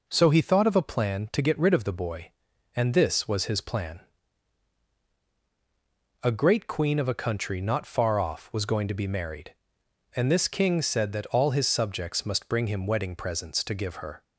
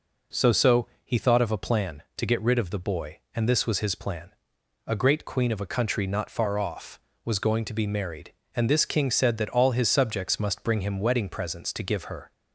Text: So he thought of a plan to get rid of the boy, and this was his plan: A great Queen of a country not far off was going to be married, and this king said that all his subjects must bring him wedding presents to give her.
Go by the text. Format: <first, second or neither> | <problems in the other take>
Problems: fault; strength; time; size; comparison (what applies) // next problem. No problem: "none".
first | says "So" twice; at 0.5 s